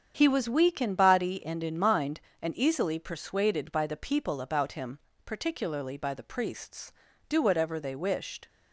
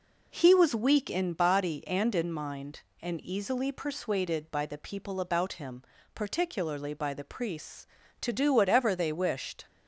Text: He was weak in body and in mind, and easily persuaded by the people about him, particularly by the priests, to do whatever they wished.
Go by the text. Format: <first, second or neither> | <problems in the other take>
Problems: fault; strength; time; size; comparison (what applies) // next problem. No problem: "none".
second | starts louder than the rest; strong; until 1.1 s; 8 dB // skips "to"; at 7.1 s